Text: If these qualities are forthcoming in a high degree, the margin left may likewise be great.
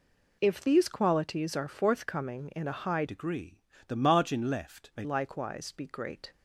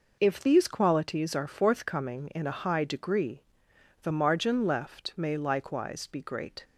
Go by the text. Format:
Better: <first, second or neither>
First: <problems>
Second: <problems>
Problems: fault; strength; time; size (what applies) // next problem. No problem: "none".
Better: second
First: changes voice from "degree" to "may"; from 3.0 to 5.0 s; 2.0 s long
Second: none